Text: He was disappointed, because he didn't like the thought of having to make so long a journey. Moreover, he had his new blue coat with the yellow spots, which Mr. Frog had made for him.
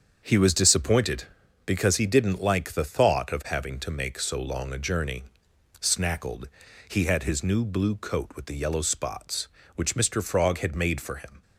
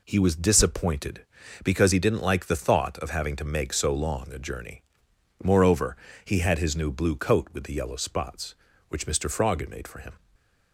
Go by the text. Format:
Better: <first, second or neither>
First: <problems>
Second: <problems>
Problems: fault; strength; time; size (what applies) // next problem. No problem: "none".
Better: second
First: starts louder than the rest; until 1.6 s; 7 dB // says "Snackled" for "Moreover"; at 5.7 s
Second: none